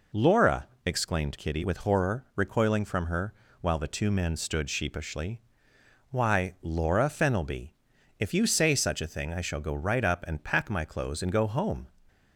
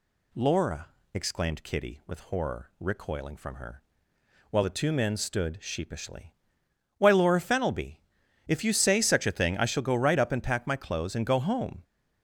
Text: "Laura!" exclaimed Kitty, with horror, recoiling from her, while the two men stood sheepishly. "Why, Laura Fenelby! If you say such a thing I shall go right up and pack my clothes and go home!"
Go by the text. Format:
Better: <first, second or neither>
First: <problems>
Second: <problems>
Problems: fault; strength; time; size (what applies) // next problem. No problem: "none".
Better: neither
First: none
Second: none